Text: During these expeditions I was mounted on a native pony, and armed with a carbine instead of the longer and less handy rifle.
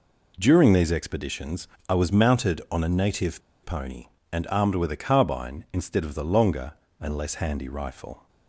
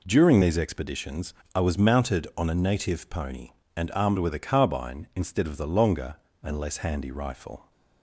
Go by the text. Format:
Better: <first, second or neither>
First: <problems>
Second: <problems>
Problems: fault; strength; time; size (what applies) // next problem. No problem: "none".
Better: second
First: pauses between "expeditions" and "I"; slight; at 1.6 s; 0.22 s long // pauses between "native" and "pony"; slight; at 3.4 s; 0.22 s long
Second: pauses between "expeditions" and "I"; slight; at 1.3 s; 0.22 s long